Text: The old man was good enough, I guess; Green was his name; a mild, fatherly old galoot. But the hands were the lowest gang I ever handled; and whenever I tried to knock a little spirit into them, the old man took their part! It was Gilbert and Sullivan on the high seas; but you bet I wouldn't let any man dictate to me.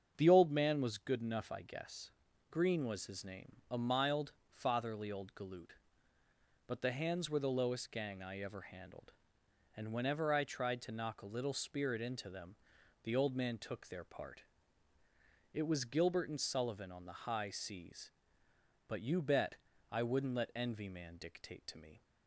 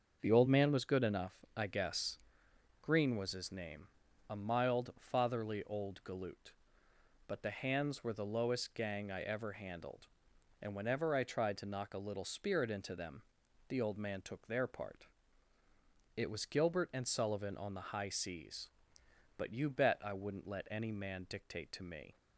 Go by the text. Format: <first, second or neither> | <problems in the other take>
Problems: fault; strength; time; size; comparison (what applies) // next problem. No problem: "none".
second | starts louder than the rest; strong; until 1.1 s; 7.5 dB; also in the second // pauses between "bet" and "I"; slight; at 19.5 s; 0.34 s long // says "envy" for "any"; at 20.5 s